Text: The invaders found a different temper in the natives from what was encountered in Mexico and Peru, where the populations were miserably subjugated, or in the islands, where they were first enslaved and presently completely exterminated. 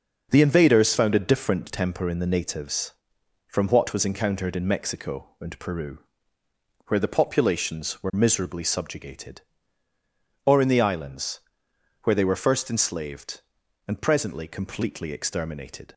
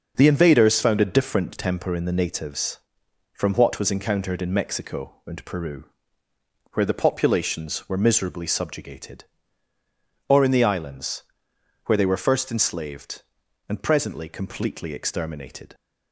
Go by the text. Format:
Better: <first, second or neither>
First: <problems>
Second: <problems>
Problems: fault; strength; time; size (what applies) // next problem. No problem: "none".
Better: neither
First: none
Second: none